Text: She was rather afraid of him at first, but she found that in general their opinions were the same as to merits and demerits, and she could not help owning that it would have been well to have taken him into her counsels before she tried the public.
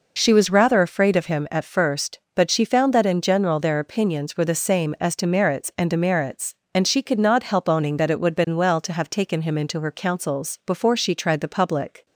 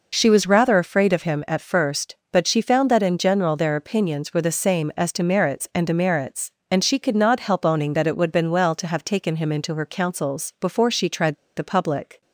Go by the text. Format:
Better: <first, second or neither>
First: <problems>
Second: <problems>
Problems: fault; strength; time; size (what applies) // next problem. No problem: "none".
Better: first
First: none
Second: pauses between "tried" and "the"; slight; at 11.3 s; 0.22 s long